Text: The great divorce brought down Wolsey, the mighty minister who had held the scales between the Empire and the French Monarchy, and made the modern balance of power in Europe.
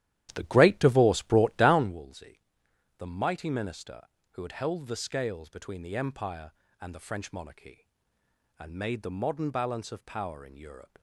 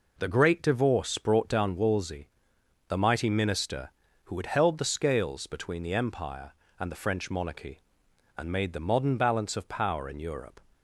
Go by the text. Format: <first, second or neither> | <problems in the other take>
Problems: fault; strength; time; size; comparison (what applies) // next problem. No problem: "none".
second | starts louder than the rest; strong; until 2.0 s; 12.5 dB